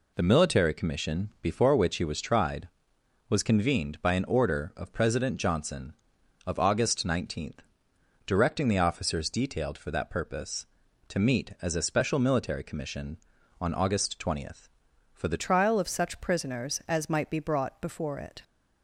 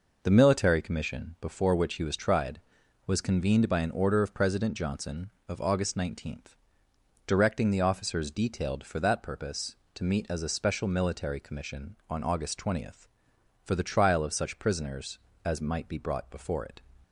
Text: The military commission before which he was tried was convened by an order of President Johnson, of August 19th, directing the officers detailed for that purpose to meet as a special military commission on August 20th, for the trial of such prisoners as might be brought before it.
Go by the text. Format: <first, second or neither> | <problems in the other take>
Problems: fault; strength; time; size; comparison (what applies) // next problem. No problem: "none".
second | changes voice at "trial"; from 15.4 s on; 3.0 s long